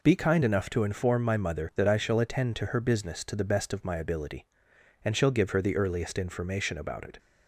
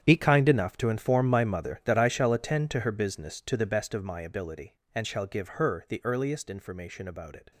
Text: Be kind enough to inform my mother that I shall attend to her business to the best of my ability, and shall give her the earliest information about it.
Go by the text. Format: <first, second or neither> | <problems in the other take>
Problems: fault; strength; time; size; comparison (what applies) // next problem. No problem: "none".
first | gets quieter; strong; throughout; 14.5 dB